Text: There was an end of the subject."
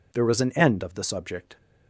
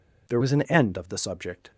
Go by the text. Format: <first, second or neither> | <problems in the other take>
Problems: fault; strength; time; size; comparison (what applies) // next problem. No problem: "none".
first | changes voice from "was" to "an"; from 0.3 to 0.6 s; 0.3 s long